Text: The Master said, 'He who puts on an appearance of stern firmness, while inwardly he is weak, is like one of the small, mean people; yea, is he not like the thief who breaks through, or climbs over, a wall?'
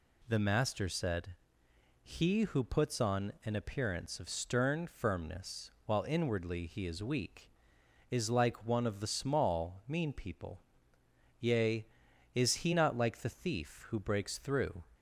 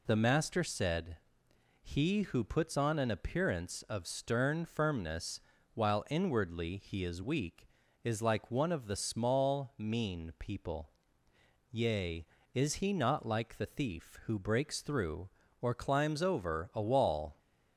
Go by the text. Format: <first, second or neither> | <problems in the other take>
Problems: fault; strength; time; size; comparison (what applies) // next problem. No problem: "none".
second | stops before "or climbs over a wall"; at 14.9 s